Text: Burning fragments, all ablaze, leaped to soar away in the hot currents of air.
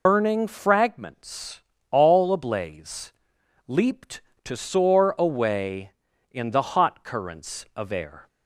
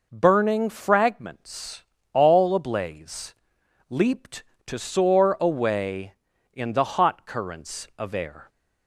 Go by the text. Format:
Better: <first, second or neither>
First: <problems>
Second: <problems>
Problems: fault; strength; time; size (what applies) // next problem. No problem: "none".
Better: second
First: loses the start of "Burning"; at 0.0 s; 165 ms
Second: none